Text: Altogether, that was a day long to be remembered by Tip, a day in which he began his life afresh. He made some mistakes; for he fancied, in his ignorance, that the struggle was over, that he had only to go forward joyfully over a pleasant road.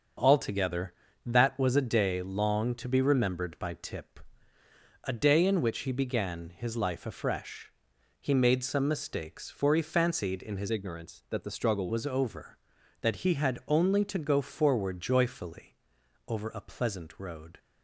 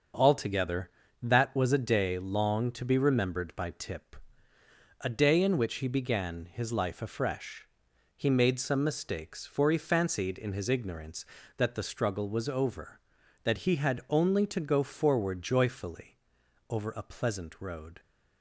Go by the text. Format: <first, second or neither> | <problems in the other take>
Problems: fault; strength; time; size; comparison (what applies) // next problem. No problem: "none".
second | starts louder than the rest; until 1.5 s; 6.5 dB; also in the second // changes voice from "ignorance" to "struggle"; from 10.7 to 11.8 s; 1.1 s long // pauses between "joyfully" and "over"; noticeable; at 15.7 s; 0.52 s long; noticeable in the second